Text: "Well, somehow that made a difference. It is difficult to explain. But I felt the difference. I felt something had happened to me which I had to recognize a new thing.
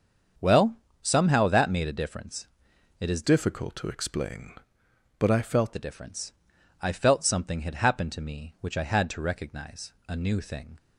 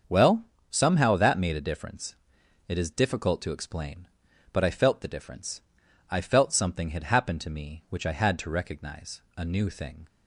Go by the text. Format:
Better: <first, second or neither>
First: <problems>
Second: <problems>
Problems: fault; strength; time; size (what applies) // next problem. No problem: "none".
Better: second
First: starts louder than the rest; strong; until 1.6 s; 7 dB // changes voice from "difficult" to "felt"; from 3.2 to 5.7 s; 2.5 s long // pauses between "recognize" and "a"; slight; at 9.9 s; 0.16 s long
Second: starts louder than the rest; until 1.3 s; 7 dB // pauses between "recognize" and "a"; slight; at 9.2 s; 0.16 s long